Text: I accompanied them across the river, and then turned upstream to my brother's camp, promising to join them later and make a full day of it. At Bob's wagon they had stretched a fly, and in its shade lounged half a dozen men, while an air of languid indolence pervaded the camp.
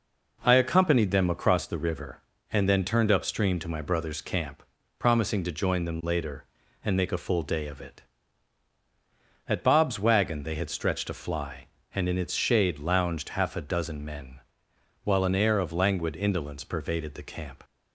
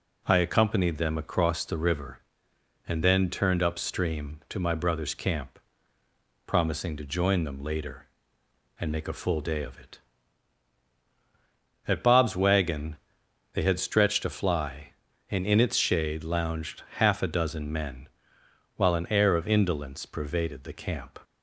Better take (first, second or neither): first